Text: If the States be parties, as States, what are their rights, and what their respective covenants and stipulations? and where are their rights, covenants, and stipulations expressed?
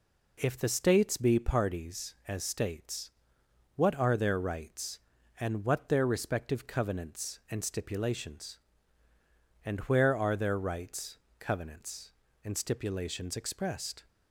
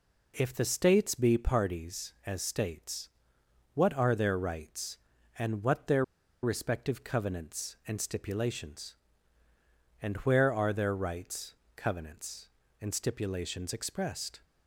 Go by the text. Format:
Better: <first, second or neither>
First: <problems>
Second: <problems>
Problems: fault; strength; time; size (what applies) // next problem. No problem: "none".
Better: first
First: none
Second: pauses between "their" and "respective"; at 6.0 s; 0.40 s long